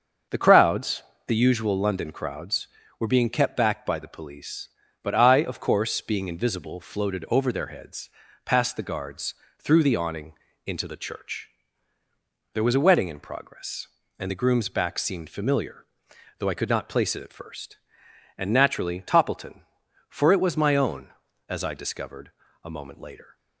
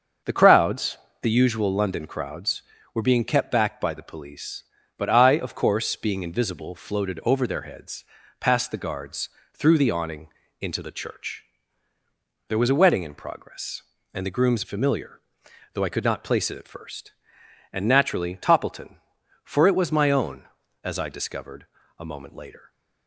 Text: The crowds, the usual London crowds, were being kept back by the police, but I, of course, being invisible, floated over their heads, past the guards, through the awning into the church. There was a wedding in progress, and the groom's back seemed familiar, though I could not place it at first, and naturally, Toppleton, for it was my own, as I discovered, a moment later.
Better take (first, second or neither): first